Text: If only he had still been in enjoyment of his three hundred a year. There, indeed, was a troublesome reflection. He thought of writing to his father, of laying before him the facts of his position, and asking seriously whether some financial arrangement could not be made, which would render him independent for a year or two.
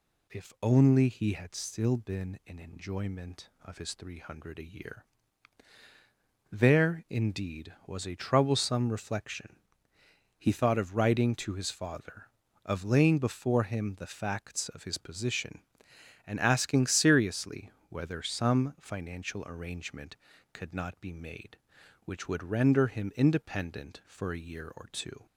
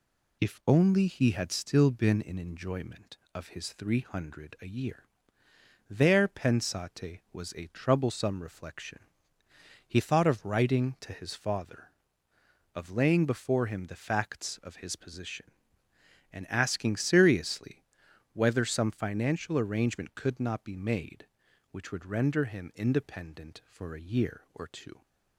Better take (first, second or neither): first